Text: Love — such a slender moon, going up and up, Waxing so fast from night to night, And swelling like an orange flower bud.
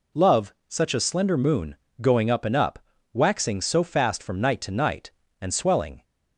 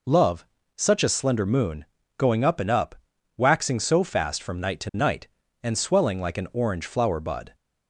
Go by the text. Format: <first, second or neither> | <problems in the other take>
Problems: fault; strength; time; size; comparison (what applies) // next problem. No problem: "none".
second | stops before "like an orange flower bud"; at 6.0 s